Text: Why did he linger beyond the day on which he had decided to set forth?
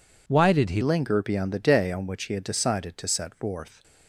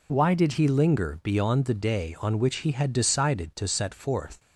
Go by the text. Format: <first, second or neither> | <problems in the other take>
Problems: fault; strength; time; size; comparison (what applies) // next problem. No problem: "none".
second | changes voice at "linger"; from 0.8 s on; 3.0 s long